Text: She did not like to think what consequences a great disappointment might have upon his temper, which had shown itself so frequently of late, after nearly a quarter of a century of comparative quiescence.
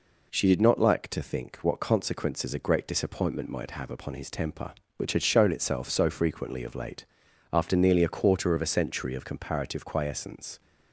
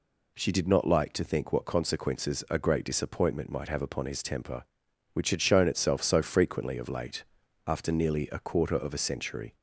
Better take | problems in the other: first | stops before "of comparative quiescence"; at 9.5 s

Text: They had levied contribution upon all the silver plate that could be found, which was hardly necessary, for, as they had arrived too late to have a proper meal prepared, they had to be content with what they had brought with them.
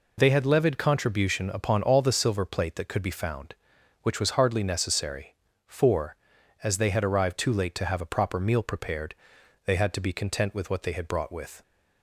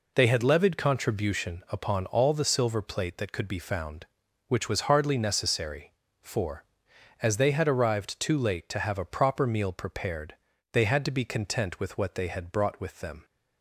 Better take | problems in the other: second | stops before "them"; at 11.6 s

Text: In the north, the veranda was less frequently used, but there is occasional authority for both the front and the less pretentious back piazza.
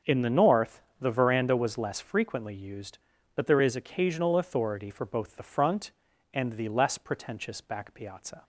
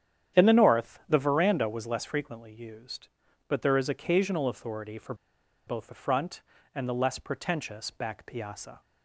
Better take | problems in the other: first | starts louder than the rest; strong; until 1.4 s; 9.5 dB; also in the first // pauses between "for" and "both"; noticeable; at 5.1 s; 0.52 s long

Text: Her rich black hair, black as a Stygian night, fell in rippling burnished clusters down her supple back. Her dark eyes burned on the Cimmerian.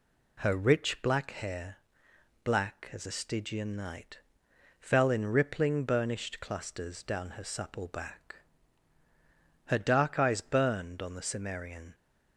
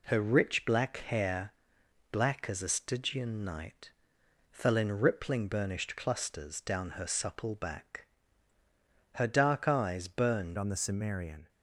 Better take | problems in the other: first | changes voice at "on"; from 10.5 s on; 0.9 s long

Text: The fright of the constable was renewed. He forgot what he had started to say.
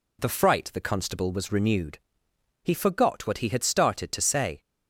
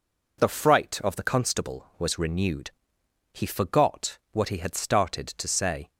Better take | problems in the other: second | skips "of"; at 0.7 s

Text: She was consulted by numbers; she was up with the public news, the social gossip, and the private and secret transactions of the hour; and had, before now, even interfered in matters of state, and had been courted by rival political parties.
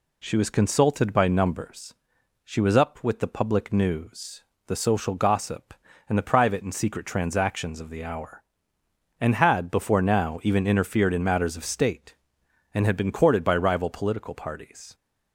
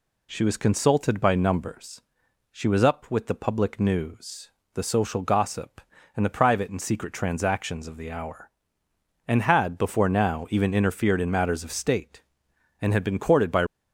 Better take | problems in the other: first | stops before "rival political parties"; at 13.6 s

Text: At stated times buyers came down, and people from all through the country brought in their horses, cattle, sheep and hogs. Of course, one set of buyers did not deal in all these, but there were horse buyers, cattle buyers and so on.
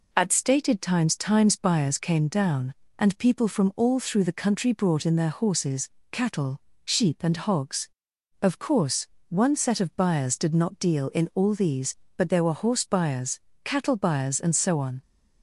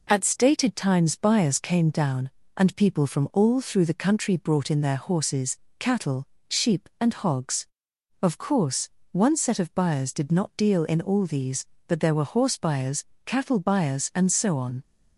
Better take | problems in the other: second | says "times" twice; at 1.1 s

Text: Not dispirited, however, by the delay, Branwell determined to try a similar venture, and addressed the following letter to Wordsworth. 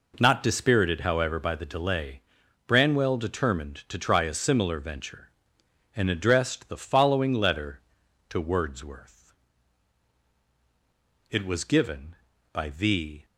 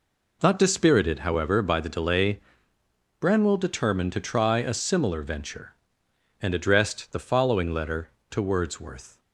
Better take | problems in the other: second | goes on to say "It was given by the"; strong; from 11.3 s on; 1.9 s long

